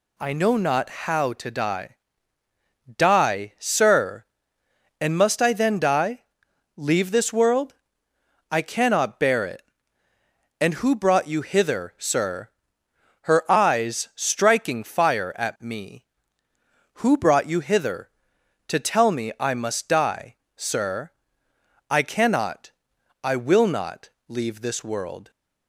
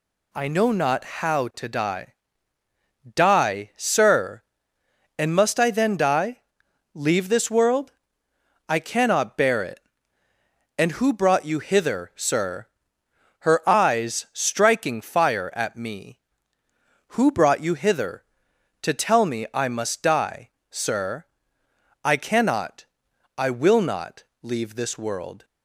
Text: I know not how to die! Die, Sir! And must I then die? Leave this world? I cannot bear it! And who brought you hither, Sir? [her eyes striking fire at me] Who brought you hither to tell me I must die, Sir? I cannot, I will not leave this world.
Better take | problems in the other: neither | pauses between "not" and "leave"; slight; the same in both

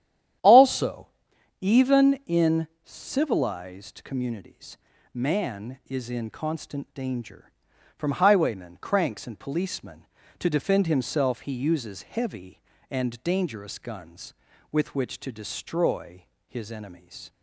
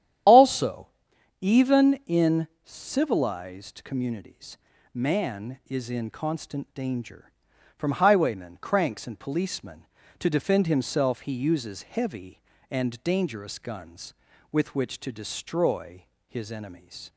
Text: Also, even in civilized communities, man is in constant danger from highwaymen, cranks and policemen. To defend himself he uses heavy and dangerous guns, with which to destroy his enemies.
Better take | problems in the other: first | loses the start of "Also"; at 0.2 s; 50 ms // starts louder than the rest; strong; until 1.7 s; 10.5 dB; strong in the first // pauses between "in" and "civilized"; slight; at 2.4 s; 0.16 s long; slight in the first // pauses between "destroy" and "his"; slight; at 16.0 s; 0.24 s long; slight in the first

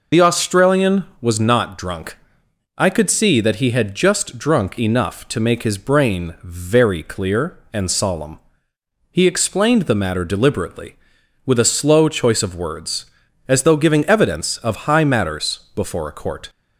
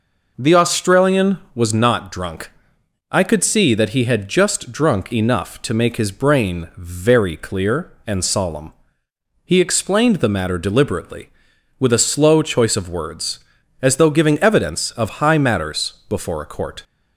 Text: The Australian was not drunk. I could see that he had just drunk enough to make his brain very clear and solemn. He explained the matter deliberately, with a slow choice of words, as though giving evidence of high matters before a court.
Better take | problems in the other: second | loses the start of "The"; at 0.1 s; 100 ms // pauses between "matters" and "before"; slight; at 15.5 s; 0.16 s long; slight in the second

